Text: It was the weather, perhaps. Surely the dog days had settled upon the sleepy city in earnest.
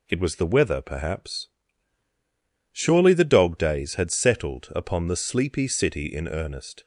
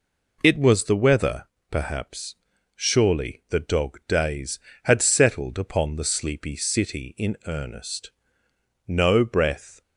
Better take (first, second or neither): first